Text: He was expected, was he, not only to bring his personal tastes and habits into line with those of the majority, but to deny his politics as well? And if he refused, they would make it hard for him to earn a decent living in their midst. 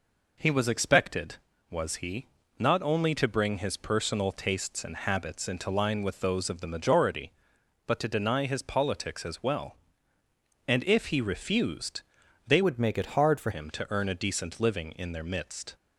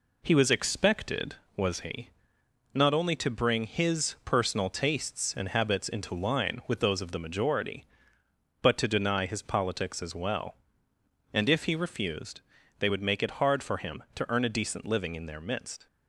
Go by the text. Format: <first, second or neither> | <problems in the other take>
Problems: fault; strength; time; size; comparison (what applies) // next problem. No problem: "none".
second | changes voice from "would" to "for"; from 12.6 to 13.5 s; 0.9 s long